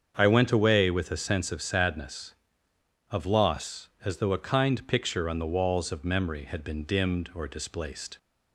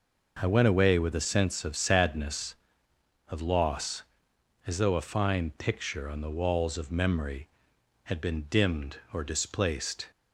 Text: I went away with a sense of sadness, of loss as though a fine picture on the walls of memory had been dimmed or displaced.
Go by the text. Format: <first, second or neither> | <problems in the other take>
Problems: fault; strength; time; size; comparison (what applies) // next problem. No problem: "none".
second | starts louder than the rest; strong; until 1.1 s; 7 dB // says "kind" for "fine"; at 4.4 s